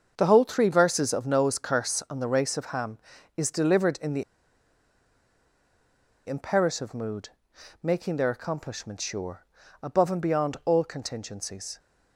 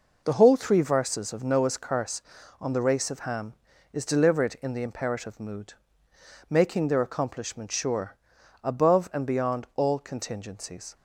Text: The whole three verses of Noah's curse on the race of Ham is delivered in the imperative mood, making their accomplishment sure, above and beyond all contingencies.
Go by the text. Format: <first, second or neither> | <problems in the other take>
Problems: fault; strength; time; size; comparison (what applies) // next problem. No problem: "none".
second | starts louder than the rest; until 1.2 s; 6.5 dB // pauses between "the" and "imperative"; strong; at 4.2 s; 2.0 s long